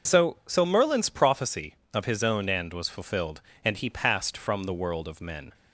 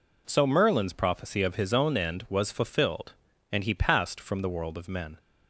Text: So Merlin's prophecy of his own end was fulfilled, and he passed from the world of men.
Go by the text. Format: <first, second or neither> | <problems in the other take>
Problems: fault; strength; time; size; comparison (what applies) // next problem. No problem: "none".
second | says "So" twice; at 0.4 s